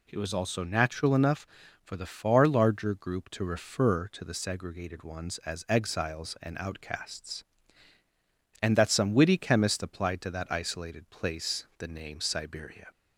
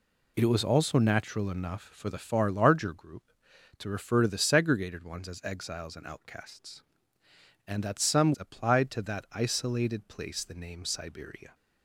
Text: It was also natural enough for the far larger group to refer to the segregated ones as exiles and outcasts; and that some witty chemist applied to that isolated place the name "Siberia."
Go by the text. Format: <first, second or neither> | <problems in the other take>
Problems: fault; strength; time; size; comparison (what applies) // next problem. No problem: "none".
first | skips "witty chemist"; at 8.3 s